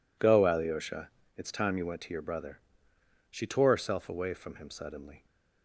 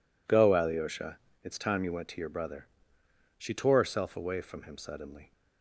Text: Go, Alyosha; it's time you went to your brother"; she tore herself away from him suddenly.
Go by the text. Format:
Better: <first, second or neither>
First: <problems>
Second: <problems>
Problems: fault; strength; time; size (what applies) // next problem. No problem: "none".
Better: neither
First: none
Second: none